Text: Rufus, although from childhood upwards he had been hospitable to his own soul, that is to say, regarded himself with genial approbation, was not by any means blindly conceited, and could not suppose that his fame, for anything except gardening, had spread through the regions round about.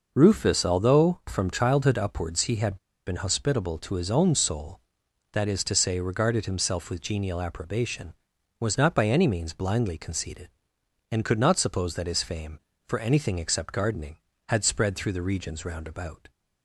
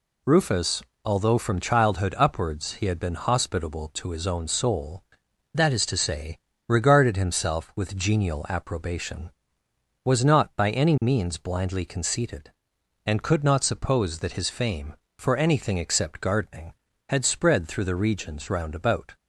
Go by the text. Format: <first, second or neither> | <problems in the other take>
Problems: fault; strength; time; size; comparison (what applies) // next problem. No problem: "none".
second | pauses between "had" and "been"; slight; at 2.7 s; 0.30 s long